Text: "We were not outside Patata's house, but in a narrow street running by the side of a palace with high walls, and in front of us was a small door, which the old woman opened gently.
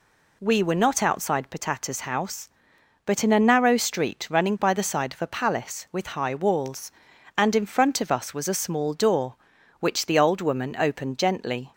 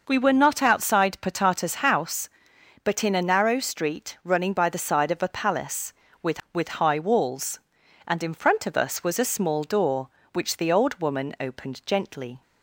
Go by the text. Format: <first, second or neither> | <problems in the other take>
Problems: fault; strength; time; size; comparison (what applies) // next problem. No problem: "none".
first | says "with" twice; at 6.5 s